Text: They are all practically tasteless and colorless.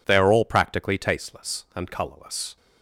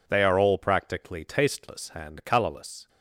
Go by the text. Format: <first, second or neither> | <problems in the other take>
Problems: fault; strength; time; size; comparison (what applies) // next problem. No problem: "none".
neither | none